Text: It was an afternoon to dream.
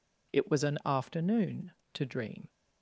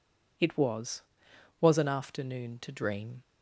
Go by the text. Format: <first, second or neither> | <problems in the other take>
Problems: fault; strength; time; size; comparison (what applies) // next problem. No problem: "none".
first | says "was" twice; at 1.6 s